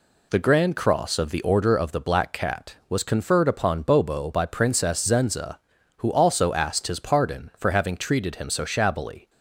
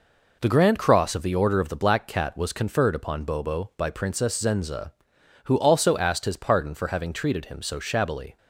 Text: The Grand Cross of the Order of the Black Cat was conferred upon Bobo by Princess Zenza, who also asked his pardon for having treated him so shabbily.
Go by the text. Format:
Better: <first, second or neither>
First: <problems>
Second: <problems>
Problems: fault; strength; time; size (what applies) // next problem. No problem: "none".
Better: neither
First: none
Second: none